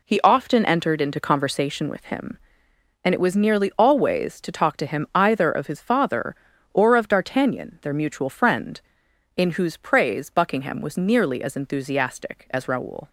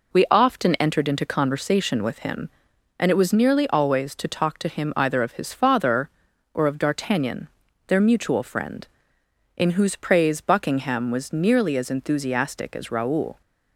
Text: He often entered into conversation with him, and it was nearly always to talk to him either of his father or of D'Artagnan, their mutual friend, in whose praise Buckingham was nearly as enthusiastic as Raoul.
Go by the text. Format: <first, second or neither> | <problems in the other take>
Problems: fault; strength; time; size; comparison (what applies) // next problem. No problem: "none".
first | says "We" for "He"; at 0.1 s